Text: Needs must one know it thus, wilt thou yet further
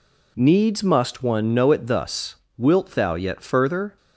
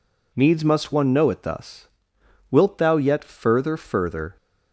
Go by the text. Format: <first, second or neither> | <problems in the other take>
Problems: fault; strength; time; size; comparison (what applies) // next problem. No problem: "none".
first | says "further" twice; at 3.7 s